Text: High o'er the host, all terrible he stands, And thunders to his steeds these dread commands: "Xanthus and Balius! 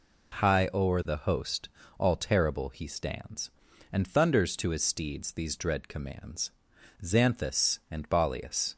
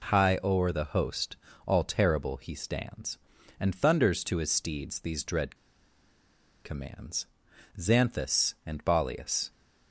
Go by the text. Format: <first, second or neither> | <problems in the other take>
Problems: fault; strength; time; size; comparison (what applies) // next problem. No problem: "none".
first | pauses between "dread" and "commands"; at 5.5 s; 1.0 s long